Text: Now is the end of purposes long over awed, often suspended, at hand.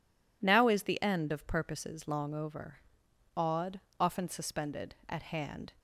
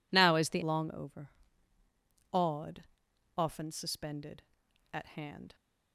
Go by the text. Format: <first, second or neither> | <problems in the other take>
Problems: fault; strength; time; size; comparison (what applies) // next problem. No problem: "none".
first | skips "end of purposes"; at 0.6 s // pauses between "over" and "awed"; at 1.3 s; 1.0 s long; noticeable in the first